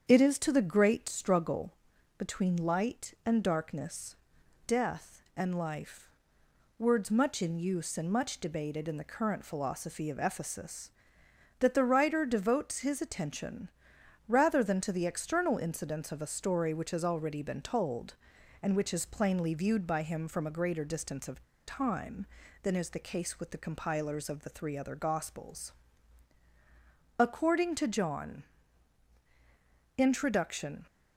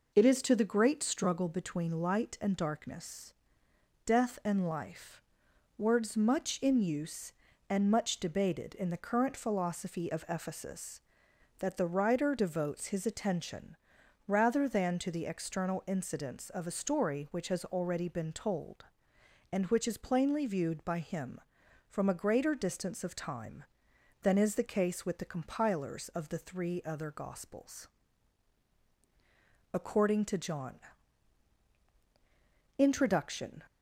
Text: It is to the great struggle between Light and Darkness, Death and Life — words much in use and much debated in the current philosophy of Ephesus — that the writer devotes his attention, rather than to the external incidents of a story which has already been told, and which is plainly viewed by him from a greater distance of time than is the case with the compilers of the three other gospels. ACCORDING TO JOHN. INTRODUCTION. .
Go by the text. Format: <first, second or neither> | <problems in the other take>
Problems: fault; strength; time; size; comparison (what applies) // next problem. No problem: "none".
second | starts louder than the rest; strong; until 1.0 s; 7.5 dB // pauses between "struggle" and "between"; at 1.7 s; 0.44 s long // pauses between "of" and "time"; slight; at 21.4 s; 0.24 s long